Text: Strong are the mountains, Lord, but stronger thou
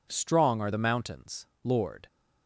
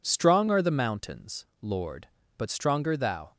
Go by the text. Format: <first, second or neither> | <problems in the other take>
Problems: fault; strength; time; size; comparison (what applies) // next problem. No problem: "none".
second | stops before "but stronger thou"; at 2.0 s